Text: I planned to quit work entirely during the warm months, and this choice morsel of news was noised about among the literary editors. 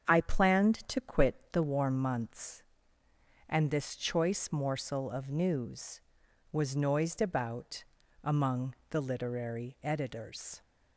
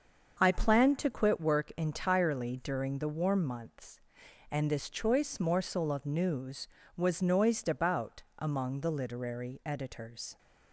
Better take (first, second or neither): second